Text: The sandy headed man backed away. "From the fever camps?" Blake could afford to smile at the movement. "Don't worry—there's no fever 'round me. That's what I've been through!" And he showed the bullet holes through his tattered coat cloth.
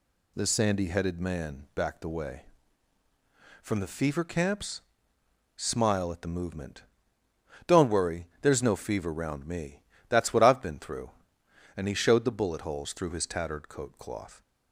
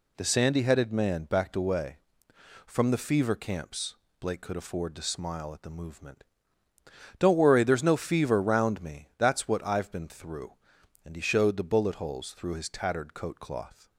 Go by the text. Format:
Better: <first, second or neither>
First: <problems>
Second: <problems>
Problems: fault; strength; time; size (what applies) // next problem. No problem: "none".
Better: second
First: skips "Blake could afford to"; at 5.1 s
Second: none